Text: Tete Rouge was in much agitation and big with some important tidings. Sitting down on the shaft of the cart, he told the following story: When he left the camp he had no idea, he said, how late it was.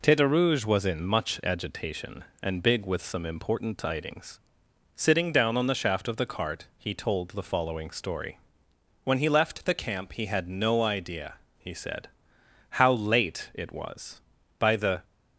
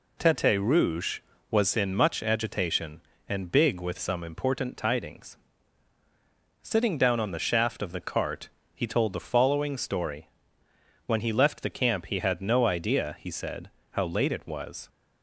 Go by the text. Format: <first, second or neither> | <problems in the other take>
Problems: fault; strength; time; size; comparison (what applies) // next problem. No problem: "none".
second | goes on to say "By the"; slight; from 14.5 s on; 0.46 s long